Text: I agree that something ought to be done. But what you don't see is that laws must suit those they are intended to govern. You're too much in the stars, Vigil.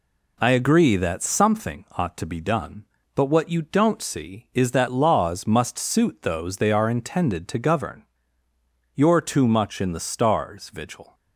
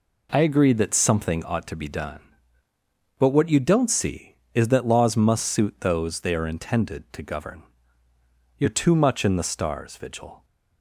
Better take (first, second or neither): neither